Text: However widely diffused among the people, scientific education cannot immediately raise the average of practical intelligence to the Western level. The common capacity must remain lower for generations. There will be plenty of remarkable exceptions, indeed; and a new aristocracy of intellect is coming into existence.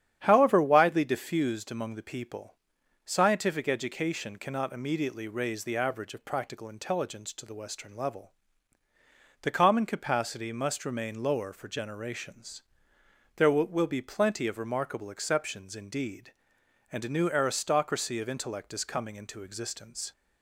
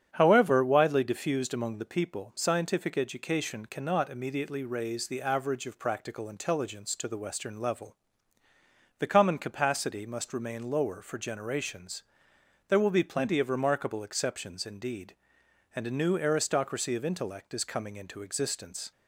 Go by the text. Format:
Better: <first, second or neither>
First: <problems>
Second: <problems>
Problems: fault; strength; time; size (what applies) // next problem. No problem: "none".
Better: second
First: starts louder than the rest; strong; until 1.2 s; 9.5 dB // says "will" twice; at 13.6 s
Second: starts louder than the rest; strong; until 1.1 s; 8.5 dB